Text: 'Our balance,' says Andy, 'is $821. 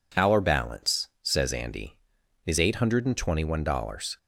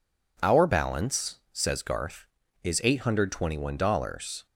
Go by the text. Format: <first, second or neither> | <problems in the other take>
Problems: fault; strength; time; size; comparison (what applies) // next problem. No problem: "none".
first | says "Garth" for "Andy"; at 1.8 s